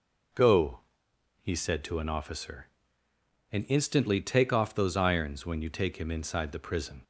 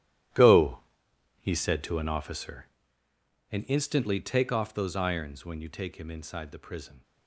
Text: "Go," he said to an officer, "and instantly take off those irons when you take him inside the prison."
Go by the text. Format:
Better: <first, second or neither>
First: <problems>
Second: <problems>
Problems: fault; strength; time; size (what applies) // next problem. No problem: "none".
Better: first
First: none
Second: gets quieter; strong; throughout; 14.5 dB